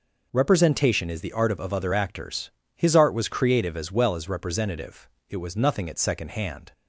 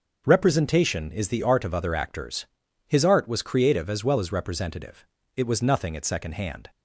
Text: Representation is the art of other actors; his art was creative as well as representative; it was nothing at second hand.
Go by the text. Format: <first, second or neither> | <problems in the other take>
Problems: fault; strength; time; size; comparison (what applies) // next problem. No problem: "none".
second | says "of" twice; at 1.6 s